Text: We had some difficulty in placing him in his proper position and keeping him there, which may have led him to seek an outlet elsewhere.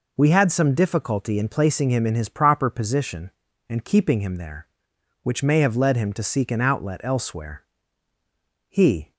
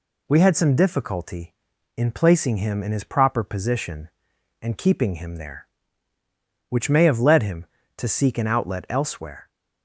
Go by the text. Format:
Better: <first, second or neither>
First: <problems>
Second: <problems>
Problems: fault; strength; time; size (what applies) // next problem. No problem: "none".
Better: second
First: goes on to say "He"; slight; from 8.6 s on; 0.44 s long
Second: none